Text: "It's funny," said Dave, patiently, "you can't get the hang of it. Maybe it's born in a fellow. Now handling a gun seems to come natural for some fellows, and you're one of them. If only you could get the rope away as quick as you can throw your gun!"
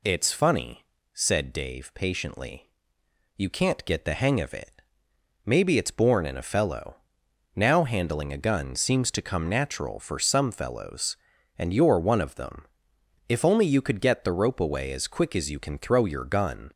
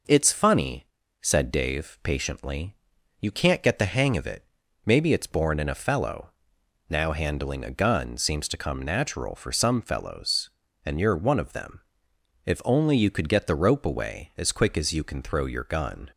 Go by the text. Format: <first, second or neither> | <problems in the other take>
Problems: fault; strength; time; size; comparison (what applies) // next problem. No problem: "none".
neither | none